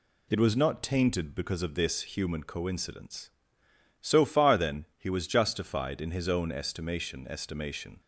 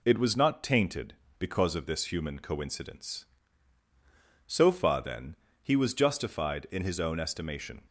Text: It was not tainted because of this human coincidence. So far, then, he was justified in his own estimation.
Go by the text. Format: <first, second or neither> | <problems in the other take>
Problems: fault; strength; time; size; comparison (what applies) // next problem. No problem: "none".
second | says "estimation" twice; at 7.2 s